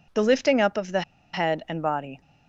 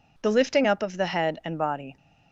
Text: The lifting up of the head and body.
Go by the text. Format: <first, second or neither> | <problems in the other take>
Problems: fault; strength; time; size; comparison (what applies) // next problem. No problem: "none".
second | pauses between "the" and "head"; slight; at 1.0 s; 0.32 s long